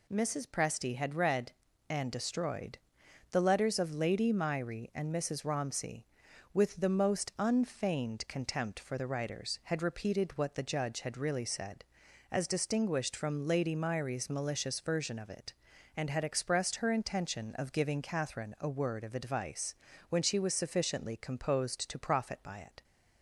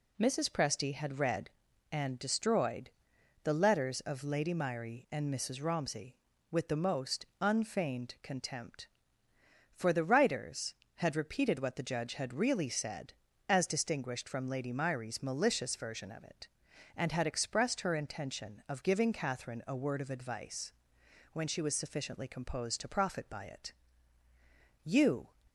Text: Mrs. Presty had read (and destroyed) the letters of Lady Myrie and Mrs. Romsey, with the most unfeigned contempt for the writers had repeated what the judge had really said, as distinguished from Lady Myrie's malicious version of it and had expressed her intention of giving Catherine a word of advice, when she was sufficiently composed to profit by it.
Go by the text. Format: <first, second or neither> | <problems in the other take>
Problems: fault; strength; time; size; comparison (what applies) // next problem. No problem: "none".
first | pauses between "most" and "unfeigned"; slight; at 7.2 s; 0.17 s long // goes on to say "You"; slight; from 24.8 s on; 0.46 s long